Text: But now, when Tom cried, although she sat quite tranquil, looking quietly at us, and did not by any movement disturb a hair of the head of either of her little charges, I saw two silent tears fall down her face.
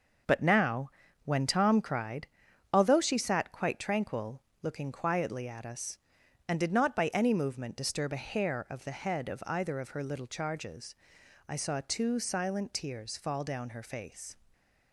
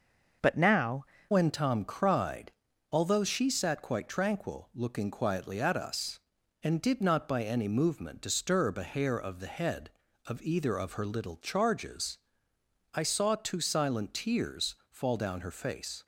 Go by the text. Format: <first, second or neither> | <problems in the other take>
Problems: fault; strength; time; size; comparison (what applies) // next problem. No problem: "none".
first | starts louder than the rest; noticeable; until 1.6 s; 6 dB // changes voice at "when"; from 1.3 s on; 14.7 s long